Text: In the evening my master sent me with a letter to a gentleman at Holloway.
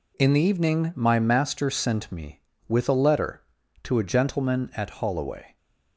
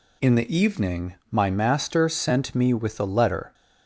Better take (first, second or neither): first